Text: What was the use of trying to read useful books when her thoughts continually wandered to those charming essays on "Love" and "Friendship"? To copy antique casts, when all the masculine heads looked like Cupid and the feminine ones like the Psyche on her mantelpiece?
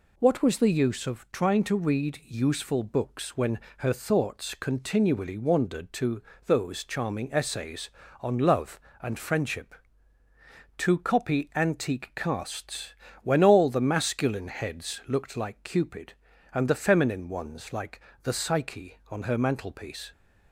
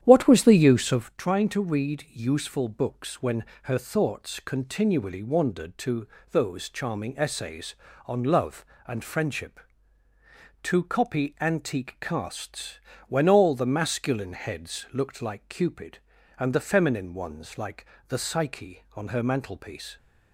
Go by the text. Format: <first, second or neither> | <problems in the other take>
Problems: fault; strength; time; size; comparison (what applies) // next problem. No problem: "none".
first | starts louder than the rest; strong; until 1.2 s; 10 dB // pauses between "when" and "her"; slight; at 3.4 s; 0.18 s long; slight in the first // pauses between "to" and "those"; slight; at 6.0 s; 0.24 s long; slight in the first // pauses between "like" and "the"; slight; at 17.8 s; 0.24 s long; slight in the first